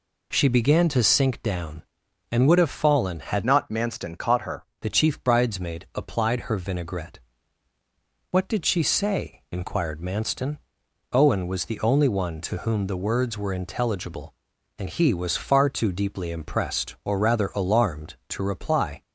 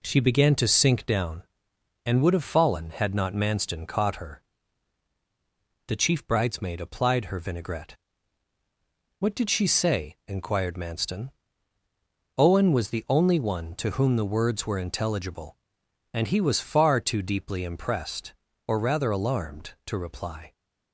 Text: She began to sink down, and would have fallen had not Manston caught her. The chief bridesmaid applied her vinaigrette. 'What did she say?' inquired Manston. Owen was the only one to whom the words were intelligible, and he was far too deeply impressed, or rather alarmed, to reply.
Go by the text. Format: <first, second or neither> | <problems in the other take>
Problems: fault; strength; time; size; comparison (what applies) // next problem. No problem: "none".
second | changes voice from "not" to "her"; from 3.4 to 4.6 s; 1.2 s long